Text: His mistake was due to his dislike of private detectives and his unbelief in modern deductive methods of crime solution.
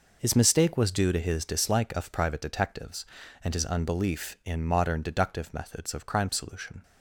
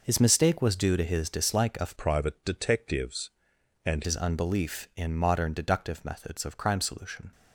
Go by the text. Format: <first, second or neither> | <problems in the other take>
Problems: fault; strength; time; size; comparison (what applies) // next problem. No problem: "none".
first | changes voice from "private" to "and"; from 1.9 to 4.0 s; 2.1 s long